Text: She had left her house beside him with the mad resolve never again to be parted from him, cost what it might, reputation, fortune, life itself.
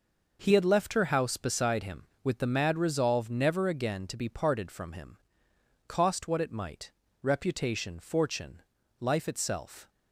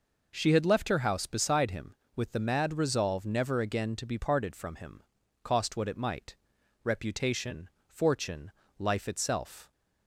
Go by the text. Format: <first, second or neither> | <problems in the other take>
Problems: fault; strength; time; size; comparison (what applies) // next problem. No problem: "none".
second | says "He" for "She"; at 0.4 s